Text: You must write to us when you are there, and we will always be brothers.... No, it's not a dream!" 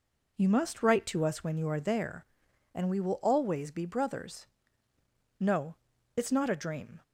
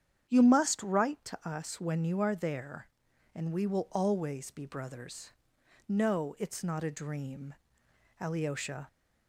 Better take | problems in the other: first | starts louder than the rest; strong; until 1.3 s; 9 dB // goes on to say "Alyosha"; noticeable; from 8.2 s on; 0.66 s long

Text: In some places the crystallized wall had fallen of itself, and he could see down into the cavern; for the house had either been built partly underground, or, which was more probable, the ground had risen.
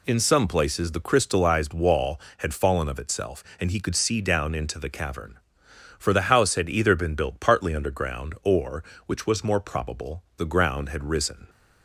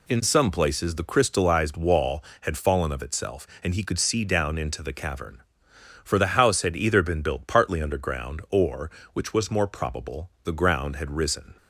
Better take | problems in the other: neither | none

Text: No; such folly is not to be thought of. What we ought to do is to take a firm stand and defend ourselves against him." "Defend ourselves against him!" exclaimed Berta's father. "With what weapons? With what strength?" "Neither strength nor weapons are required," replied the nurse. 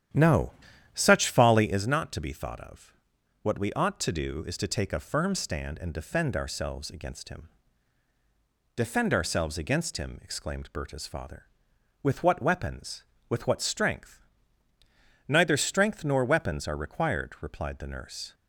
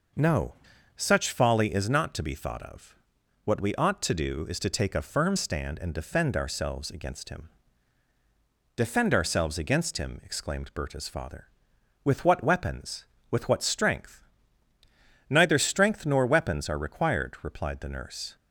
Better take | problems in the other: second | starts louder than the rest; strong; until 1.8 s; 10 dB

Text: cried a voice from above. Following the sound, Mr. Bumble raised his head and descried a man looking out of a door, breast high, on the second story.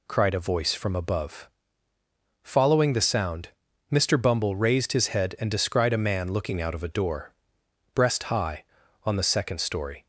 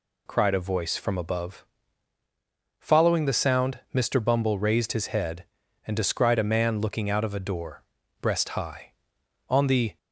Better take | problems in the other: first | stops before "second story"; at 9.9 s

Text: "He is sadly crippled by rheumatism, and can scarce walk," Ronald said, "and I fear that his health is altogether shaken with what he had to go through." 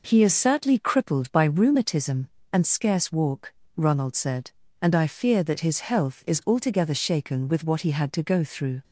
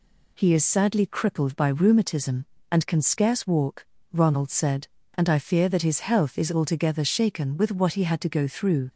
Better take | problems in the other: second | skips "can"; at 2.6 s

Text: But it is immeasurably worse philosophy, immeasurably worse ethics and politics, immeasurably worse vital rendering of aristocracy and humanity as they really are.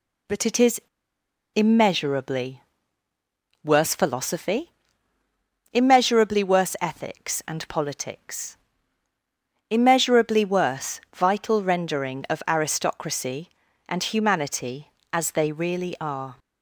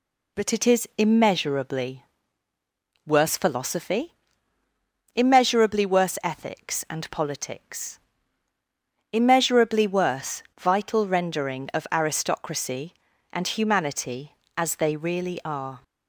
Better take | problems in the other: second | pauses between "is" and "immeasurably"; noticeable; at 0.7 s; 0.74 s long // pauses between "immeasurably" and "worse"; at 2.6 s; 1.0 s long; also in the second // pauses between "worse" and "vital"; slight; at 10.9 s; 0.16 s long; slight in the second

